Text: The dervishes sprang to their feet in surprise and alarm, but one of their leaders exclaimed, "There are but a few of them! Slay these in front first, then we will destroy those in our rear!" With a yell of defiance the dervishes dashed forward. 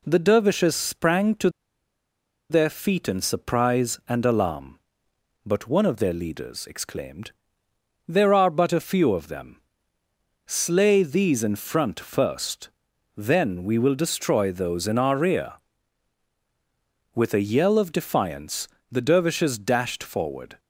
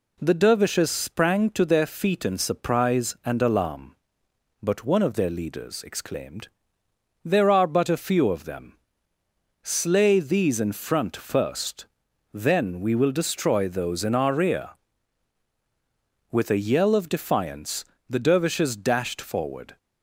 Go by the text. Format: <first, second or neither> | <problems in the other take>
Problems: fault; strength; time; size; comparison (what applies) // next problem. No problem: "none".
second | pauses between "to" and "their"; at 1.4 s; 1.0 s long // pauses between "defiance" and "the"; slight; at 18.6 s; 0.24 s long; slight in the second